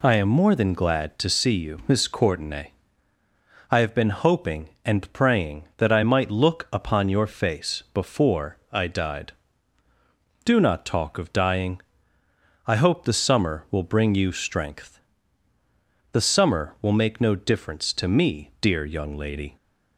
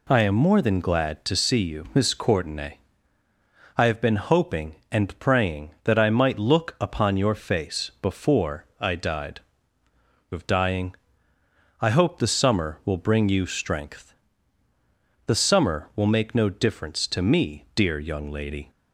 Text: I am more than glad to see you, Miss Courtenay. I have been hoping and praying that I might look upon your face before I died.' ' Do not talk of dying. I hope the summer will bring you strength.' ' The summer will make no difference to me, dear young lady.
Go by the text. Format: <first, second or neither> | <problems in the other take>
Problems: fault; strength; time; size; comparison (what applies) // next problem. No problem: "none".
first | pauses between "before" and "I"; slight; at 8.6 s; 0.16 s long; slight in the first // skips "Do not talk"; at 9.9 s